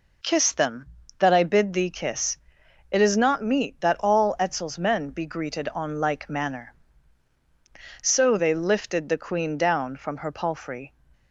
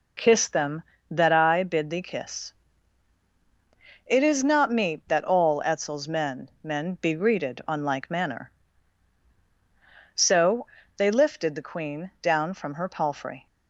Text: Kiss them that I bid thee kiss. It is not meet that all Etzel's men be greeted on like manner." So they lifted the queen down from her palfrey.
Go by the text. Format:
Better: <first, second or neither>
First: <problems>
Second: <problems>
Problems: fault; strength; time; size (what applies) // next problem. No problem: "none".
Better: first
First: none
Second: says "men" twice; at 6.6 s // pauses between "So" and "they"; slight; at 10.6 s; 0.30 s long